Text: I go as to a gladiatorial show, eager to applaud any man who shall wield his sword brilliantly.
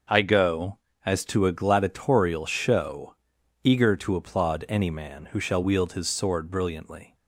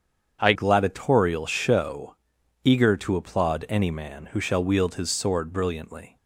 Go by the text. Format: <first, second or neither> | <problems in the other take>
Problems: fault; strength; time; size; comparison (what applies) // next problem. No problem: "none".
first | starts louder than the rest; strong; until 1.4 s; 7.5 dB; also in the first // skips "go as to a"; at 0.5 s